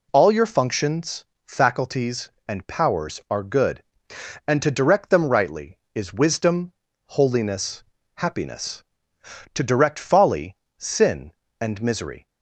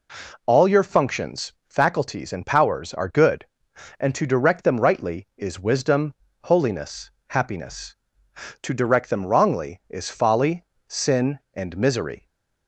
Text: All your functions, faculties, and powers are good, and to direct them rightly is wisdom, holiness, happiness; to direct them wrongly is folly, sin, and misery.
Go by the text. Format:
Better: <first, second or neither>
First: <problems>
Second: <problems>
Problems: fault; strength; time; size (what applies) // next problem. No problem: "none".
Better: second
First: skips "them wrongly is"; at 9.9 s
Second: none